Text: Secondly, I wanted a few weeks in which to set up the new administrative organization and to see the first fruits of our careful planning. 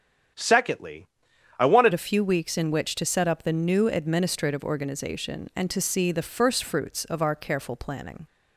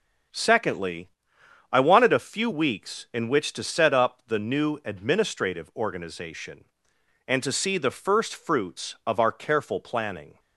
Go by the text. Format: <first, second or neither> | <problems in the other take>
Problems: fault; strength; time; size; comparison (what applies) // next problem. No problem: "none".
second | starts louder than the rest; strong; until 1.8 s; 9 dB // changes voice at "a"; from 1.9 s on; 6.3 s long